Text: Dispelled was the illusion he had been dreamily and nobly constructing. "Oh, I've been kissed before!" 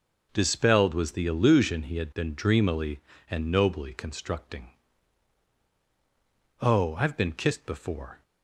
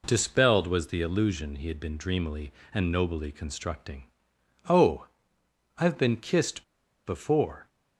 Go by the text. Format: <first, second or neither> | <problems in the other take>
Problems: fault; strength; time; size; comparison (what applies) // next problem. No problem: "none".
first | pauses between "kissed" and "before"; at 6.6 s; 0.43 s long